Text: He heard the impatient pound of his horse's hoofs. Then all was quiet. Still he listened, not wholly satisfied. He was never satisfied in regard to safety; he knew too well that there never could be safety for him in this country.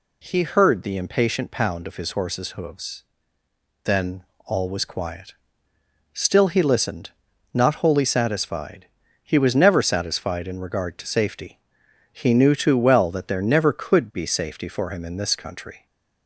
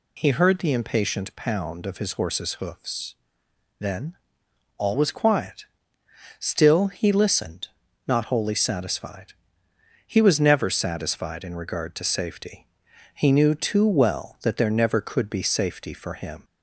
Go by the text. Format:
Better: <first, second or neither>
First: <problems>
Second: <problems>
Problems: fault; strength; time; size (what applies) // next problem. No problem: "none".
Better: first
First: pauses between "Then" and "all"; slight; at 4.2 s; 0.22 s long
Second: pauses between "Then" and "all"; noticeable; at 4.1 s; 0.60 s long // stops before "in this country"; at 16.4 s